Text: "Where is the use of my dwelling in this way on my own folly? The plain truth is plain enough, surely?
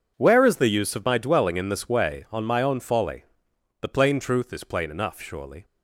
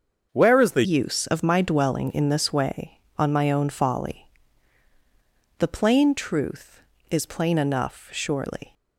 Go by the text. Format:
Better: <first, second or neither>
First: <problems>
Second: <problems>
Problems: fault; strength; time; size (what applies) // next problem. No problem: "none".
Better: first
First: none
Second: starts louder than the rest; until 1.3 s; 6.5 dB // changes voice at "use"; from 0.8 s on; 7.9 s long